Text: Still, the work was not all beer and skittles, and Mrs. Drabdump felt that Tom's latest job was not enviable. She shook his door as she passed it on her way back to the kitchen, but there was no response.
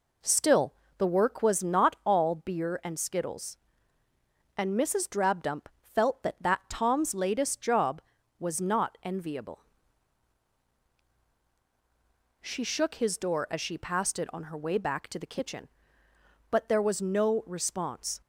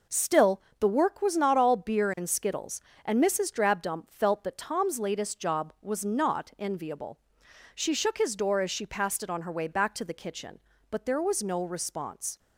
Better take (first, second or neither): second